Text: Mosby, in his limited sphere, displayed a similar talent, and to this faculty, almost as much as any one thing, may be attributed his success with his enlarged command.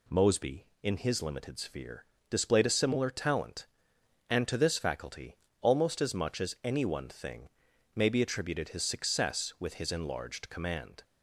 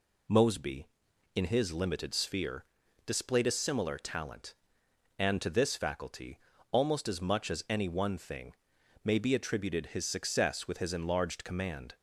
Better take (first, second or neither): neither